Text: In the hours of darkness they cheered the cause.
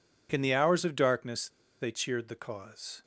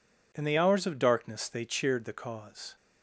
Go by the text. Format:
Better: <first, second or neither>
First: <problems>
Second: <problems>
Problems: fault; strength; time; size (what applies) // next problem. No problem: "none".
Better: second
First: pauses between "darkness" and "they"; slight; at 1.4 s; 0.32 s long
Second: none